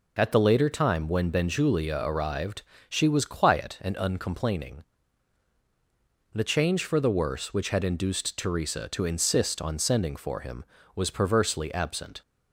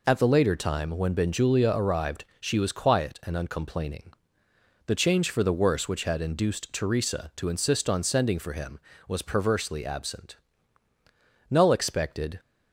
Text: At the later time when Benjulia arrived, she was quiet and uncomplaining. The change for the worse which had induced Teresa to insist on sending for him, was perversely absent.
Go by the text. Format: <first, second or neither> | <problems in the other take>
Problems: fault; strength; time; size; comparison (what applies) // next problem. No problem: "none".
first | goes on to say "Null expected"; noticeable; from 11.4 s on; 0.91 s long